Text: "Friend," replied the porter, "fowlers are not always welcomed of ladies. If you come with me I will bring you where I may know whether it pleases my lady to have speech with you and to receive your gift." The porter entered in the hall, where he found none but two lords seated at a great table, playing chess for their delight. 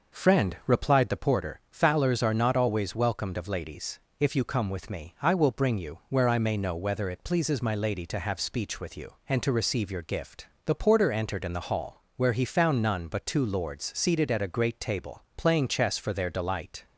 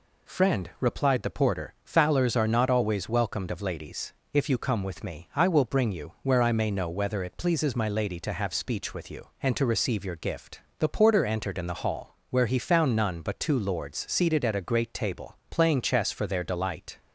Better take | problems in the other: second | starts louder than the rest; noticeable; until 1.2 s; 5.5 dB

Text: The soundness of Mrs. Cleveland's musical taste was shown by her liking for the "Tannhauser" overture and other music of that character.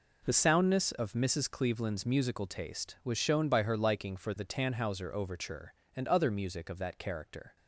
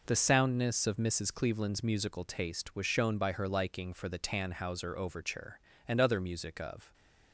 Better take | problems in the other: first | stops before "that character"; at 6.9 s

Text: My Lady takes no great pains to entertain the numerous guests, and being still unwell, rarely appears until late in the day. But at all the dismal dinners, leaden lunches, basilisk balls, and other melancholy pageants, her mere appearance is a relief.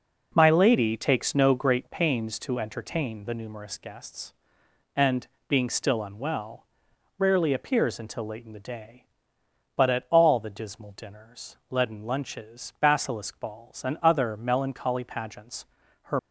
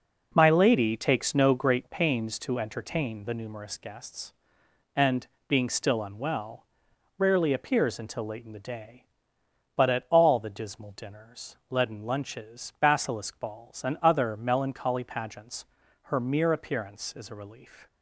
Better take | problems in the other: second | pauses between "and" and "being"; slight; at 5.2 s; 0.20 s long; slight in the second // stops before "mere appearance is a relief"; at 16.1 s

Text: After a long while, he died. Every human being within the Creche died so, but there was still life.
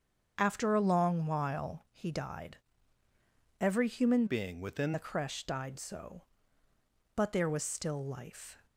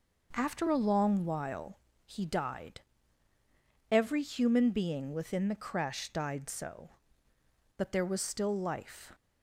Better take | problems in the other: second | starts louder than the rest; strong; until 1.3 s; 7.5 dB // changes voice from "being" to "within"; from 4.2 to 4.9 s; 0.7 s long

